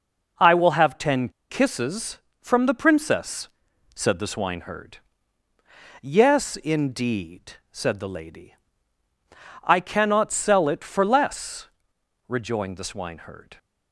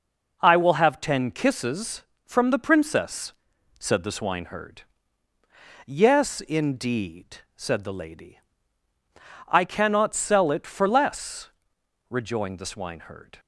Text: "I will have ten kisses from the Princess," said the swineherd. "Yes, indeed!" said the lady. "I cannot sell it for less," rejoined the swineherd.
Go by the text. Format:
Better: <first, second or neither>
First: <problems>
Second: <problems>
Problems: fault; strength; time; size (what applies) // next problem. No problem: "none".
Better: second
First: pauses between "ten" and "kisses"; slight; at 1.2 s; 0.20 s long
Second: none